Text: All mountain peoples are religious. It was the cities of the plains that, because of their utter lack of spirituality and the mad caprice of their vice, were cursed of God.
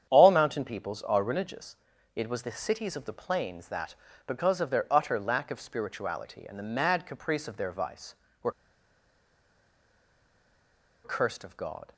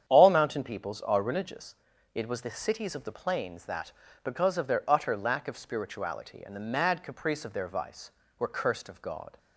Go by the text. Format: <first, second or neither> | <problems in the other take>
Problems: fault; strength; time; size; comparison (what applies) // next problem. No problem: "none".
second | starts louder than the rest; strong; until 1.1 s; 8.5 dB; strong in the second // pauses between "were" and "cursed"; strong; at 8.5 s; 2.5 s long